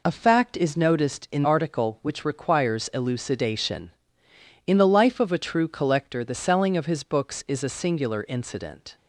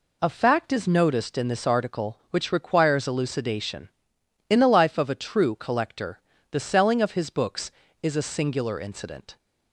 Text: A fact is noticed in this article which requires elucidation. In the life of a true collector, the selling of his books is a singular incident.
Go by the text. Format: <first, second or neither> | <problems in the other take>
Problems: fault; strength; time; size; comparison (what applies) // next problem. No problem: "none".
second | skips "this"; at 1.4 s